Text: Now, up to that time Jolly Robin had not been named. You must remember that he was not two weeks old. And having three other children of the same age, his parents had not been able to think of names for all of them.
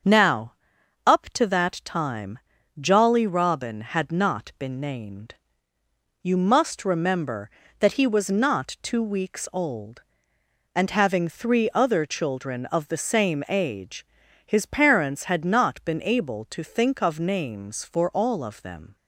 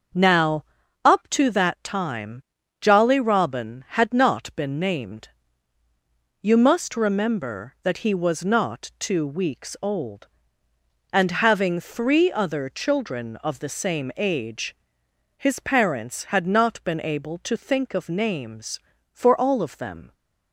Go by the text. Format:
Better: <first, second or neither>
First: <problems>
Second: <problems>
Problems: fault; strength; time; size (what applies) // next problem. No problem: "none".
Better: neither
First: starts louder than the rest; until 1.6 s; 6.5 dB // pauses between "time" and "Jolly"; at 2.3 s; 0.40 s long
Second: starts louder than the rest; until 1.5 s; 6.5 dB // pauses between "time" and "Jolly"; at 2.4 s; 0.38 s long